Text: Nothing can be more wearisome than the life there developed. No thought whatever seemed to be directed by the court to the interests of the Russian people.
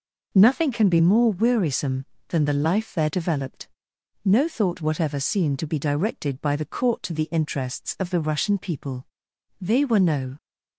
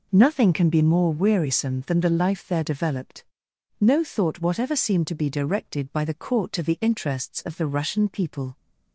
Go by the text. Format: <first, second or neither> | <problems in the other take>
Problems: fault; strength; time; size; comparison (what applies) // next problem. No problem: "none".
second | goes on to say "They were no"; noticeable; from 9.6 s on; 0.76 s long